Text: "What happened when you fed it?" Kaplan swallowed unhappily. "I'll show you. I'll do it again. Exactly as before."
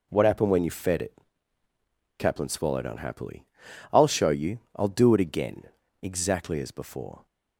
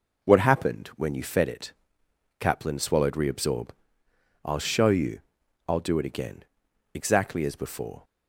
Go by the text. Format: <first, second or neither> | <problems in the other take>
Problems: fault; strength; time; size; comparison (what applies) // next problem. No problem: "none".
first | says "reabsorb" for "unhappily"; at 3.1 s